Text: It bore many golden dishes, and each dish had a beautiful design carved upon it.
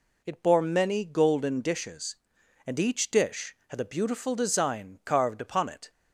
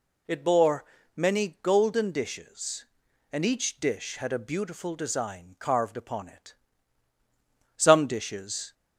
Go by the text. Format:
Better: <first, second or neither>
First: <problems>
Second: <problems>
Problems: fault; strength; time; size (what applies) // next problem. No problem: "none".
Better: first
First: none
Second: pauses between "bore" and "many"; slight; at 0.8 s; 0.30 s long // goes on to say "Some dishes"; noticeable; from 7.7 s on; 0.96 s long